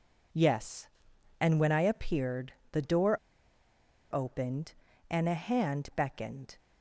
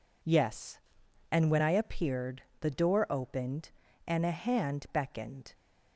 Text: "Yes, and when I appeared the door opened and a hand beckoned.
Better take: second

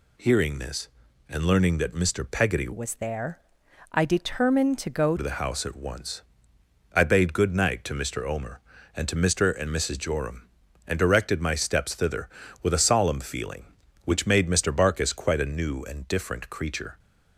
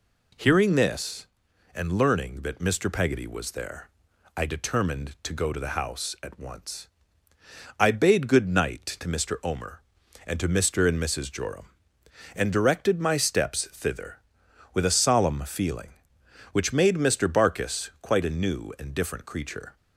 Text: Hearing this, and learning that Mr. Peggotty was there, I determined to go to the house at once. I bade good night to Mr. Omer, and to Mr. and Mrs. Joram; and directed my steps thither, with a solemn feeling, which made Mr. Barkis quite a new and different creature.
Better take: second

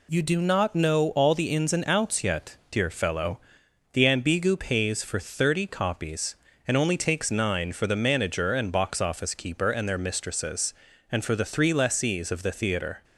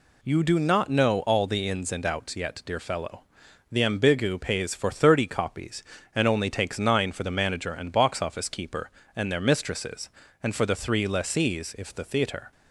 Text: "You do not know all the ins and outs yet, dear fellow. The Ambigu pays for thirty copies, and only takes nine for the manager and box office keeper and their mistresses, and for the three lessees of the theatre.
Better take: first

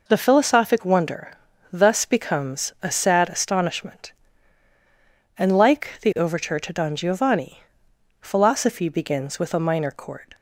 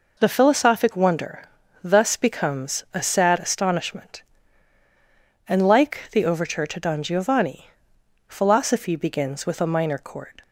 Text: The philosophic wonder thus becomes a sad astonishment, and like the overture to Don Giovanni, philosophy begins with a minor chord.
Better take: neither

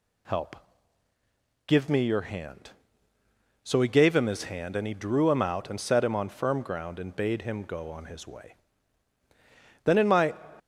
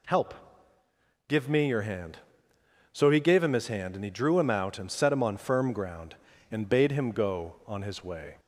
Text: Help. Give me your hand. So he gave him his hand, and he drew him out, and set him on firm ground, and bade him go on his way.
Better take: second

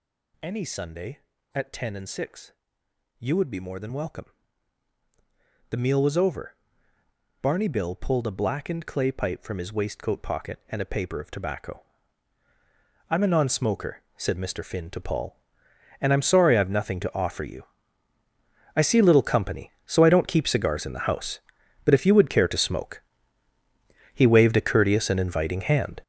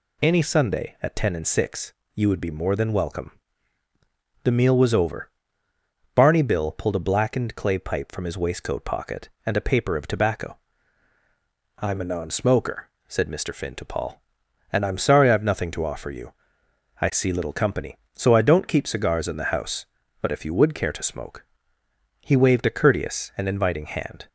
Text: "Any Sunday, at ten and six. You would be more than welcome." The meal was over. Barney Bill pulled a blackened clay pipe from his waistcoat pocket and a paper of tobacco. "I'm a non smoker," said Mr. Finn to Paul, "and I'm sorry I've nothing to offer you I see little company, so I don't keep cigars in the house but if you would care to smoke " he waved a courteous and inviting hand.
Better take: second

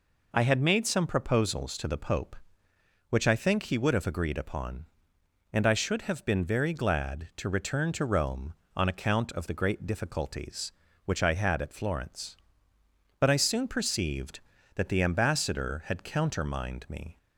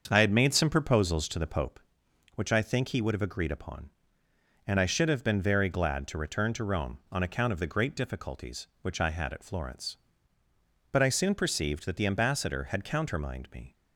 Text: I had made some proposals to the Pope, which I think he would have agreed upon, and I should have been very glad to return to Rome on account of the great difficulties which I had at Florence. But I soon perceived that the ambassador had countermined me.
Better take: first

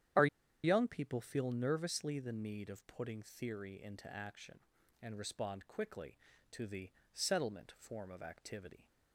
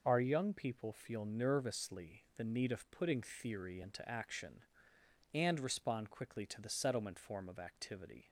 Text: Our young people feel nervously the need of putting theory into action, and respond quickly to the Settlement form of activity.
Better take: second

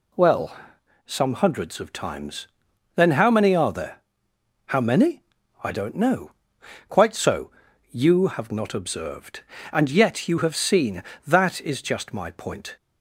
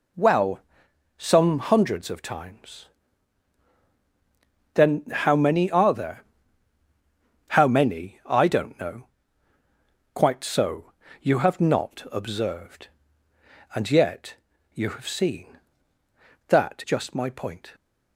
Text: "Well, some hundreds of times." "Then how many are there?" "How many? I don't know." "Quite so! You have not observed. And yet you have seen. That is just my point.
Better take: first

